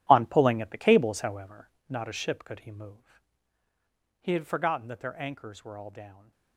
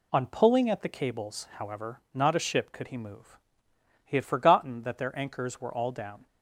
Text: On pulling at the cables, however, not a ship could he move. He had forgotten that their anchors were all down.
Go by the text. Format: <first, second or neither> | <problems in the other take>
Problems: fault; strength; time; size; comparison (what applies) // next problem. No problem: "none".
second | gets quieter; strong; throughout; 12.5 dB